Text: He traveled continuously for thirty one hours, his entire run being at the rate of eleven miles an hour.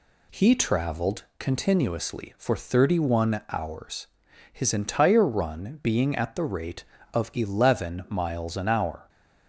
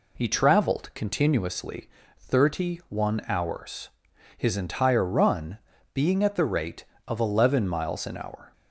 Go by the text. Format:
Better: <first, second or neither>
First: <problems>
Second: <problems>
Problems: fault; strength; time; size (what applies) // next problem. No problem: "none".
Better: first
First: none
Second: skips "for"; at 2.0 s // pauses between "run" and "being"; slight; at 5.5 s; 0.34 s long